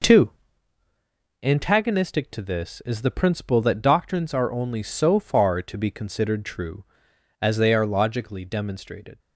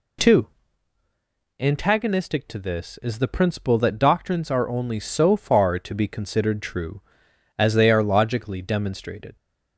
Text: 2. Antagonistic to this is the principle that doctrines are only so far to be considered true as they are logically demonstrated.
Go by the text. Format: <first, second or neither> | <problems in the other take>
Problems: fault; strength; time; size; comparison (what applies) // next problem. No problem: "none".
second | gets quieter; strong; throughout; 7 dB